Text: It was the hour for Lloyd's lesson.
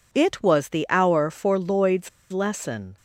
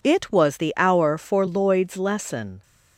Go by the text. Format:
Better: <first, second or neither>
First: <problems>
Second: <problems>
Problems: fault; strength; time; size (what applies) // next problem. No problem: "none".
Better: second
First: pauses between "Lloyd's" and "lesson"; slight; at 2.0 s; 0.23 s long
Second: none